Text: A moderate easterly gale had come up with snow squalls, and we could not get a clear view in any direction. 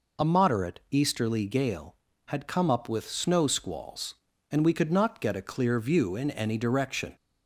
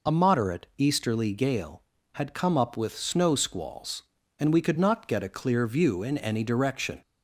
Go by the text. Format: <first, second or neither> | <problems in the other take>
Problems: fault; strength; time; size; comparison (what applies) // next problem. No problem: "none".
neither | none